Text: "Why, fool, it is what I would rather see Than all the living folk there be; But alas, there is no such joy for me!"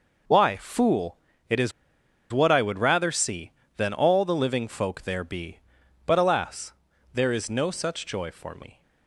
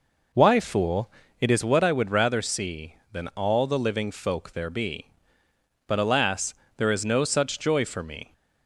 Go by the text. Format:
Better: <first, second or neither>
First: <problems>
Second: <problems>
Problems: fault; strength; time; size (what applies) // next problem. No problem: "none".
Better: second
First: pauses between "is" and "what"; noticeable; at 1.7 s; 0.60 s long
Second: none